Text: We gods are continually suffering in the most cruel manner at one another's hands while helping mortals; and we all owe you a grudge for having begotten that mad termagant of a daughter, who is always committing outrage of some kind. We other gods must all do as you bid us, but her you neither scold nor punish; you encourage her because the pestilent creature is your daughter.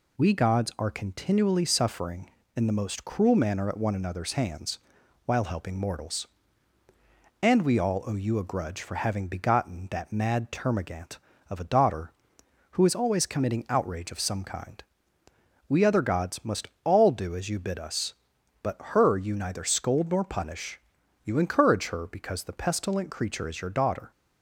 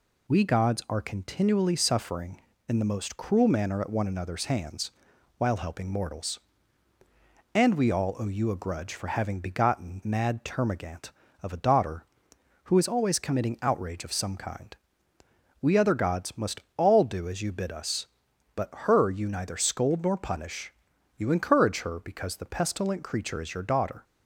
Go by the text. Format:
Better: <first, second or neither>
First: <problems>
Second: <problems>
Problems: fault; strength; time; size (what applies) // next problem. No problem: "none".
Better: first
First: pauses between "hands" and "while"; noticeable; at 4.7 s; 0.46 s long // pauses between "must" and "all"; slight; at 16.6 s; 0.16 s long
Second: pauses between "hands" and "while"; noticeable; at 4.9 s; 0.46 s long // skips "that"; at 10.0 s // pauses between "must" and "all"; slight; at 16.5 s; 0.16 s long